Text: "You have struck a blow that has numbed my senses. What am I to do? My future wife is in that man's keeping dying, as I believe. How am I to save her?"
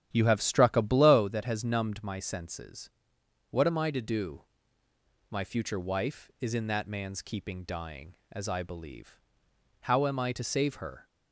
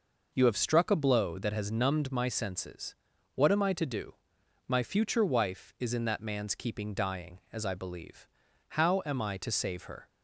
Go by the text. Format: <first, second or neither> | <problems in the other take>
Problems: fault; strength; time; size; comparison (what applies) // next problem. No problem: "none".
second | starts louder than the rest; strong; until 1.2 s; 10.5 dB